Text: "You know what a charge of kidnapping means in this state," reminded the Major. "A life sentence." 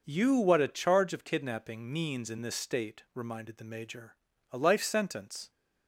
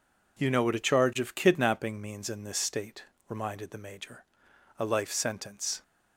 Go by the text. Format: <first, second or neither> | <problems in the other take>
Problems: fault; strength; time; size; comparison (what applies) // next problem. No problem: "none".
second | skips "know"; at 0.3 s